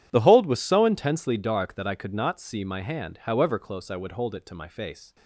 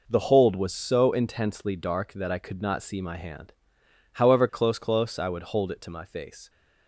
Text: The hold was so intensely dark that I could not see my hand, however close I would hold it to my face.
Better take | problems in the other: first | says "close" twice; at 4.7 s

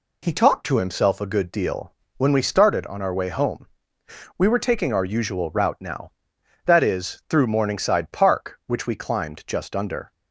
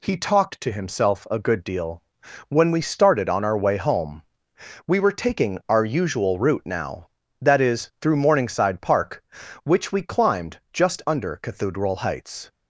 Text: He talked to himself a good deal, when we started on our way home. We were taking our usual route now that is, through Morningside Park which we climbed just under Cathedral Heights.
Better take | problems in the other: second | stops before "Cathedral Heights"; at 10.1 s

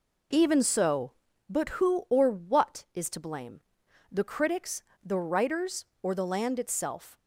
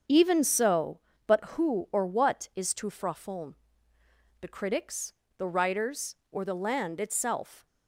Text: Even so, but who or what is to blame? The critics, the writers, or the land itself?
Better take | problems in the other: first | starts louder than the rest; until 1.3 s; 7 dB // says "frafon" for "blame"; at 2.8 s

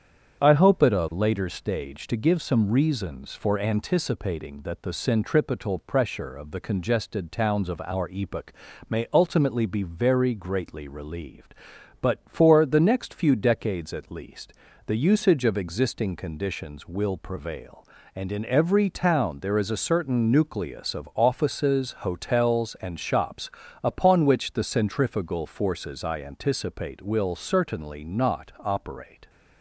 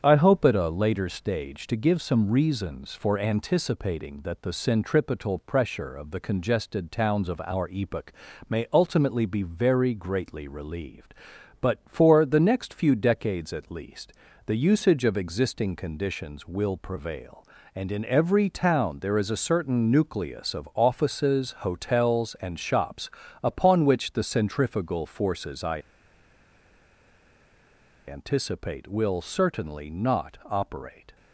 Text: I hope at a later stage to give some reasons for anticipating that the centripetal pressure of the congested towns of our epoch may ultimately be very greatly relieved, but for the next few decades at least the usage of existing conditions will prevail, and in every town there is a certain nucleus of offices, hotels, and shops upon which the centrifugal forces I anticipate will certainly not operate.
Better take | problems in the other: first | starts louder than the rest; strong; until 1.0 s; 8 dB; strong in the first // pauses between "epoch" and "may"; slight; at 8.1 s; 0.34 s long; slight in the first // pauses between "least" and "the"; slight; at 14.1 s; 0.32 s long; slight in the first // pauses between "shops" and "upon"; slight; at 23.0 s; 0.34 s long; slight in the first // pauses between "I" and "anticipate"; strong; at 25.8 s; 2.2 s long

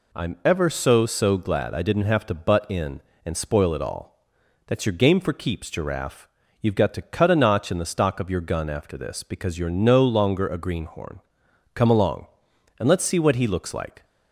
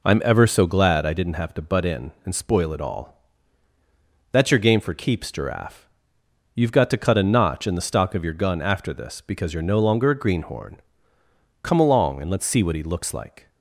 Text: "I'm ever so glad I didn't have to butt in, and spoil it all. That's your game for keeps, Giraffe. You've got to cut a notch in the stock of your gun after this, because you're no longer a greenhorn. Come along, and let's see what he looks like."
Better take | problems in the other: second | says "so" twice; at 1.0 s

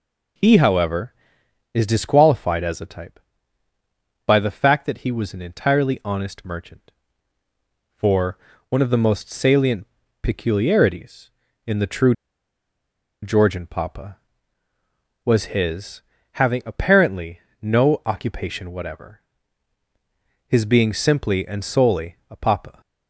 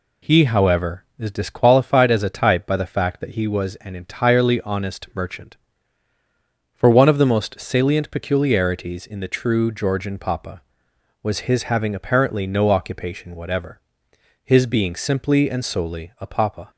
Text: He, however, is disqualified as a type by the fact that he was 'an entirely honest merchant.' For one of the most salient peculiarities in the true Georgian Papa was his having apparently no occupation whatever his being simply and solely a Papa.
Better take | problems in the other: second | pauses between "For" and "one"; slight; at 8.3 s; 0.32 s long // pauses between "salient" and "peculiarities"; slight; at 9.8 s; 0.34 s long // pauses between "true" and "Georgian"; at 12.1 s; 1.0 s long // pauses between "his" and "having"; slight; at 16.0 s; 0.32 s long // pauses between "apparently" and "no"; slight; at 17.4 s; 0.20 s long // pauses between "whatever" and "his"; strong; at 19.2 s; 1.2 s long; noticeable in the second

